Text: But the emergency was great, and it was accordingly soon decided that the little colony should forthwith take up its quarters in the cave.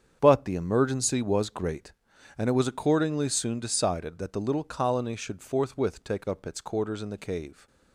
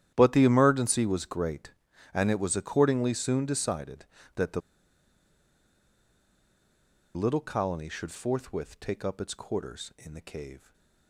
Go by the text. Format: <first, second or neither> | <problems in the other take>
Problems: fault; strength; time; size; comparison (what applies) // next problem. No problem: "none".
first | starts louder than the rest; strong; until 1.1 s; 11 dB; strong in the first // pauses between "the" and "little"; strong; at 4.6 s; 2.5 s long // stays silent after the last word; slight; from 10.5 s on; 0.5 s long